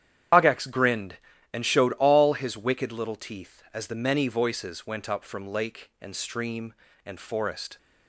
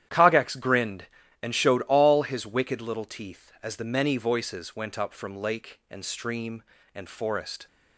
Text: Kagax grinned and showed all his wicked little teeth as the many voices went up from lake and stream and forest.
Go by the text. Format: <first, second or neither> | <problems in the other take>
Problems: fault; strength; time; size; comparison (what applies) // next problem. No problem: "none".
second | loses the start of "Kagax"; at 0.3 s; 110 ms // starts louder than the rest; strong; until 1.7 s; 10 dB; strong in the second